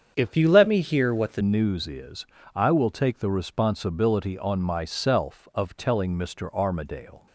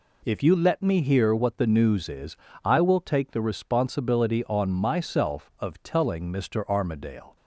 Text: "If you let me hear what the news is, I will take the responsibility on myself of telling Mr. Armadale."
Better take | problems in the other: second | starts louder than the rest; strong; until 1.1 s; 7.5 dB // changes voice from "you" to "the"; from 0.3 to 1.4 s; 1.1 s long

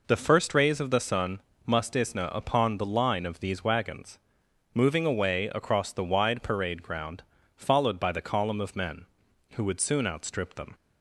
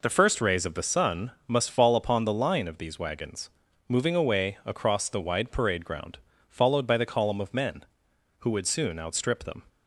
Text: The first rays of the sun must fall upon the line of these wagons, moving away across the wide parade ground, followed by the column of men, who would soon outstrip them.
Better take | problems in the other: second | pauses between "sun" and "must"; slight; at 1.4 s; 0.24 s long; slight in the second // says "isna" for "fall"; at 1.9 s

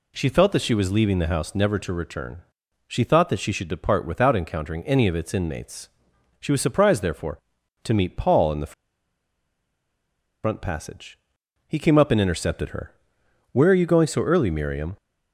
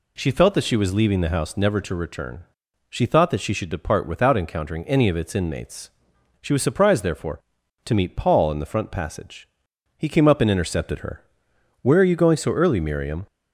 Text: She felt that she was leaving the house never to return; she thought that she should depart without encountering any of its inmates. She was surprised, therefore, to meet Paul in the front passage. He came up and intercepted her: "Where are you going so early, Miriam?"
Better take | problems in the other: second | pauses between "the" and "front"; strong; at 8.7 s; 1.7 s long

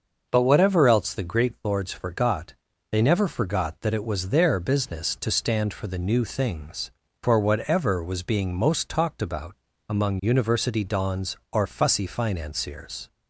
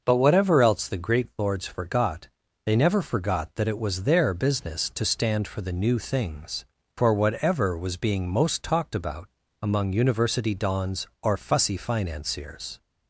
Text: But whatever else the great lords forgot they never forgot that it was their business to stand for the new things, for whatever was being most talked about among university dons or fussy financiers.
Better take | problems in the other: neither | starts louder than the rest; noticeable; the same in both // pauses between "forgot" and "they"; the same in both // pauses between "about" and "among"; slight; the same in both

